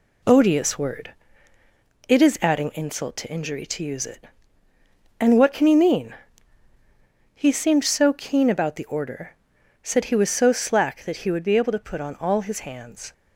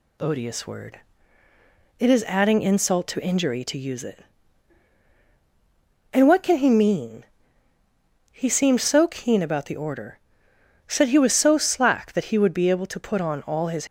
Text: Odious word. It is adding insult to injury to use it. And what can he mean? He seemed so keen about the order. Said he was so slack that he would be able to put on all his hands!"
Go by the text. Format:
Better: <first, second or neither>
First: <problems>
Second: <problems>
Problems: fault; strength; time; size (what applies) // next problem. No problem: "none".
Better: first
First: none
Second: stops before "hands"; at 13.8 s